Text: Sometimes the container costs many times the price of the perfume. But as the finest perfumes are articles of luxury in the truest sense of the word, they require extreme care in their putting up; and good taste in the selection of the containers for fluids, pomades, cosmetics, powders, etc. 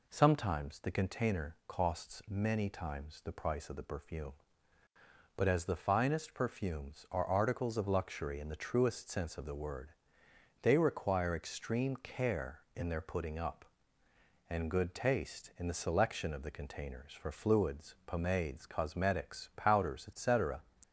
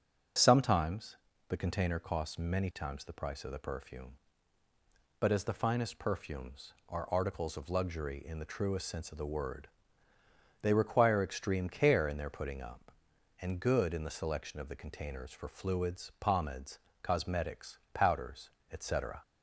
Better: first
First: none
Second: starts louder than the rest; until 1.7 s; 6 dB // pauses between "Sometimes" and "the"; slight; at 1.1 s; 0.34 s long // skips "taste"; at 13.9 s

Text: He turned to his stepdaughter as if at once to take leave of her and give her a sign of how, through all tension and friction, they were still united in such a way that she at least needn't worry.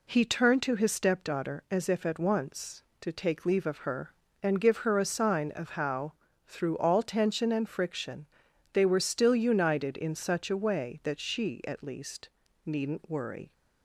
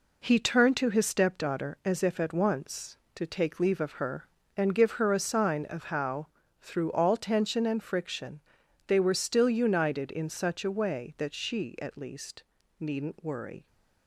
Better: first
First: pauses between "least" and "needn't"; slight; at 12.3 s; 0.34 s long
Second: gets quieter; strong; throughout; 7 dB // pauses between "least" and "needn't"; slight; at 12.4 s; 0.34 s long

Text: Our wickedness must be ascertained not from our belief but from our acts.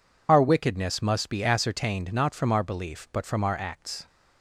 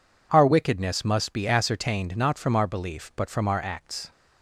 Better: second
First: loses the start of "Our"; at 0.2 s; 25 ms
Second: none

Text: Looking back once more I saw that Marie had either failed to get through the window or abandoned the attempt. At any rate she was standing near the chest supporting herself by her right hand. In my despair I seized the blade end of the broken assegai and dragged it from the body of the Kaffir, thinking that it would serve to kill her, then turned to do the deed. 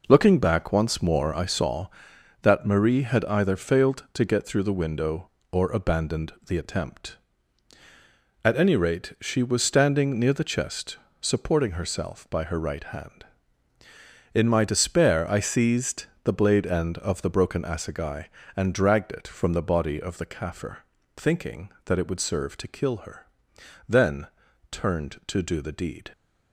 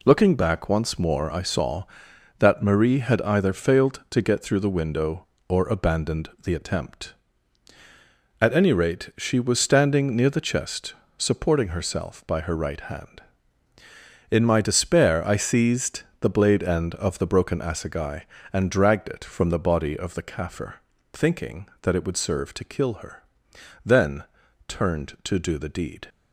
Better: second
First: starts louder than the rest; noticeable; until 1.7 s; 5 dB // pauses between "chest" and "supporting"; slight; at 10.9 s; 0.24 s long // pauses between "seized" and "the"; slight; at 16.0 s; 0.18 s long // pauses between "then" and "turned"; at 24.2 s; 0.44 s long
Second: pauses between "chest" and "supporting"; slight; at 10.9 s; 0.24 s long // pauses between "seized" and "the"; slight; at 16.0 s; 0.18 s long // pauses between "then" and "turned"; at 24.2 s; 0.44 s long

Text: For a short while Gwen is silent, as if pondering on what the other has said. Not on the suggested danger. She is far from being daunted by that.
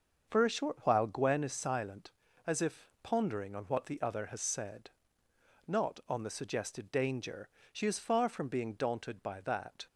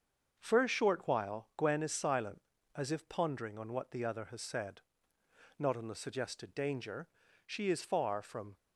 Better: first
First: starts louder than the rest; until 1.3 s; 6.5 dB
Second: starts louder than the rest; until 1.4 s; 6.5 dB // stops before "being daunted by that"; at 8.5 s

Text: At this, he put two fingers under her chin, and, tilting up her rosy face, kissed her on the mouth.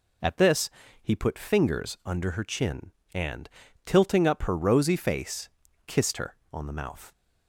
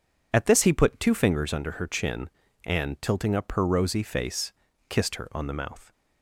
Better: second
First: skips "two"; at 1.3 s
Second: none

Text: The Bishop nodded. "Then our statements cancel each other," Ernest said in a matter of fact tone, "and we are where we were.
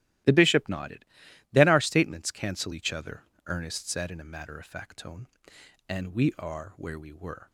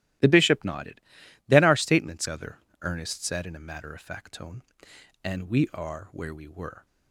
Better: first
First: starts louder than the rest; strong; until 1.7 s; 15.5 dB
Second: starts louder than the rest; strong; until 1.7 s; 15.5 dB // skips "cancel each"; at 2.2 s

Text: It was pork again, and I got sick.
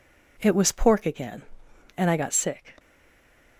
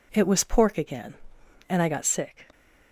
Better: second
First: stays silent after the last word; slight; from 2.7 s on; 0.8 s long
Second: none

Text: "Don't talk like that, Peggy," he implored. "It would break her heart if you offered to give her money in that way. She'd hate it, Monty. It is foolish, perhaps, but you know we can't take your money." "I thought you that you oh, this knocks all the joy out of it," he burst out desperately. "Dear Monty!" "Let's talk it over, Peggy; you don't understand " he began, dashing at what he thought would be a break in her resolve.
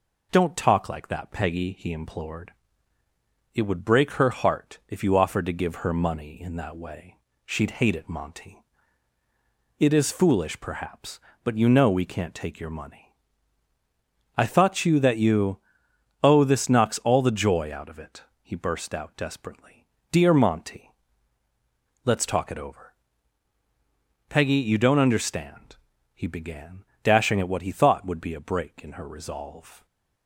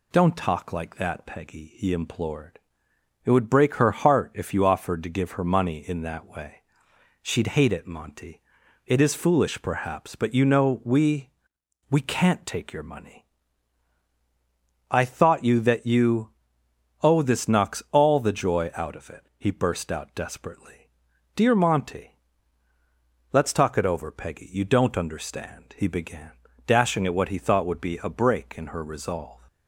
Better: first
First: pauses between "you" and "oh"; noticeable; at 15.5 s; 0.64 s long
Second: says "we" twice; at 11.9 s // pauses between "you" and "oh"; noticeable; at 16.3 s; 0.72 s long

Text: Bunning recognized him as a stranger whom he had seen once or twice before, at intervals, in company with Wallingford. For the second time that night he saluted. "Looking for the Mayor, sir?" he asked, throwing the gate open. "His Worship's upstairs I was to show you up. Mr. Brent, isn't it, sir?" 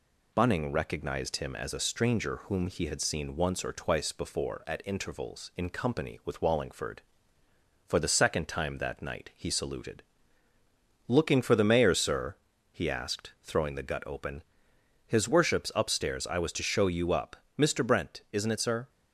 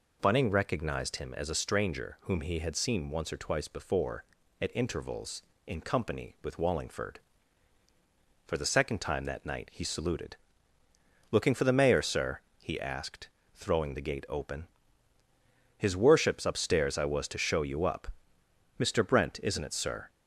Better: second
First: says "gut" for "gate"; at 13.8 s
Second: none

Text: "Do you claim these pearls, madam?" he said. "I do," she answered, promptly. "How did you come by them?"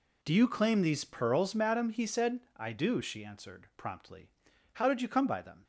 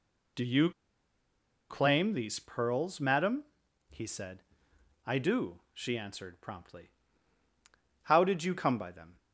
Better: first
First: none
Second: pauses between "you" and "claim"; at 0.7 s; 0.99 s long

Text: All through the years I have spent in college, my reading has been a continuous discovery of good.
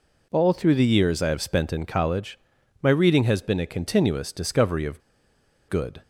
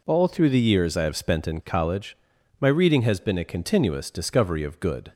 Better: second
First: pauses between "of" and "good"; noticeable; at 5.0 s; 0.68 s long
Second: none

